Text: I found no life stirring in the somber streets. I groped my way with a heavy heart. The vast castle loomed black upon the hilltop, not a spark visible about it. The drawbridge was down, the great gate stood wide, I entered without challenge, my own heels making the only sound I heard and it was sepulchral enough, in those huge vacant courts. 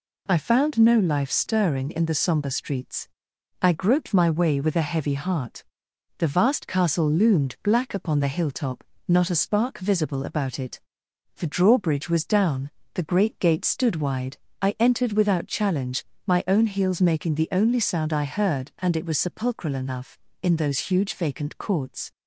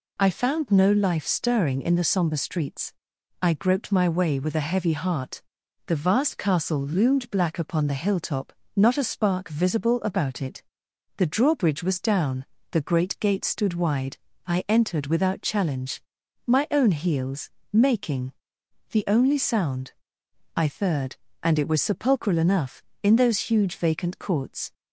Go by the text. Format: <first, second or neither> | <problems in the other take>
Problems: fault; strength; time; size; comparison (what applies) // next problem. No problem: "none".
first | pauses between "heels" and "making"; slight; at 17.4 s; 0.26 s long // pauses between "making" and "the"; noticeable; at 18.3 s; 0.58 s long // pauses between "sound" and "I"; noticeable; at 19.9 s; 0.62 s long // says "third" for "heard"; at 20.6 s